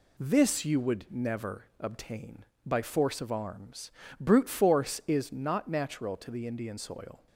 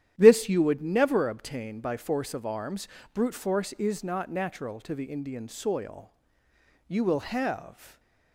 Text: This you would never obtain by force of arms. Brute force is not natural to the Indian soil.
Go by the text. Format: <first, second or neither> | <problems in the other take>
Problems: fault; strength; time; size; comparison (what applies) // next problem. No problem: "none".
first | starts louder than the rest; strong; until 1.1 s; 11 dB // goes on to say "You will have"; noticeable; from 6.8 s on; 1.1 s long // stays silent after the last word; slight; from 7.7 s on; 0.6 s long